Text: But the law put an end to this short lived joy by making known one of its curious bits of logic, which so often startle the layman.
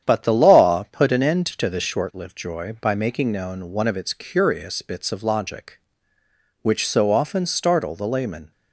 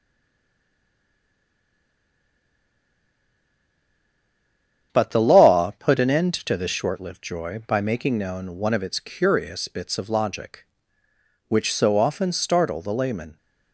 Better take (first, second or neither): first